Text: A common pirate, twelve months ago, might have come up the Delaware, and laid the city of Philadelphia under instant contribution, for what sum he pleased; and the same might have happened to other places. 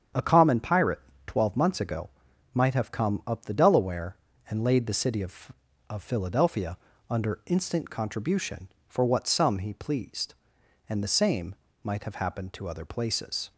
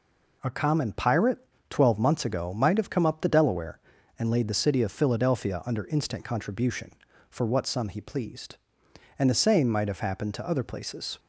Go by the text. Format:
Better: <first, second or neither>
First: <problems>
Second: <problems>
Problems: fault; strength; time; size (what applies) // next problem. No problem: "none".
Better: second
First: starts louder than the rest; strong; until 1.4 s; 8 dB // says "of" twice; at 5.8 s // pauses between "Philadelphia" and "under"; slight; at 6.7 s; 0.32 s long // pauses between "same" and "might"; slight; at 11.5 s; 0.28 s long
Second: none